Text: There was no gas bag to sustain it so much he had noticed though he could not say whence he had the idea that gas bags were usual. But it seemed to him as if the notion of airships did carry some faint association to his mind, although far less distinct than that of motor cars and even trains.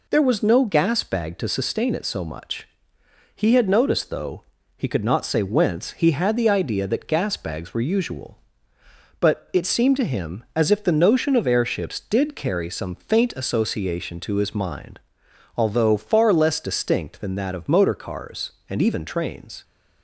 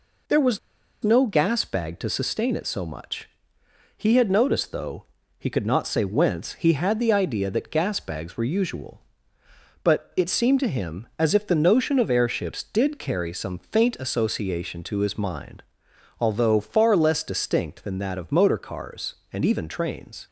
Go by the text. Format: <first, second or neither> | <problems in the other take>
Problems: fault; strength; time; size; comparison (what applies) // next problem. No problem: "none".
first | pauses between "was" and "no"; at 0.5 s; 0.45 s long // pauses between "much" and "he"; noticeable; at 3.2 s; 0.68 s long; noticeable in the first // pauses between "though" and "he"; slight; at 5.0 s; 0.34 s long; slight in the first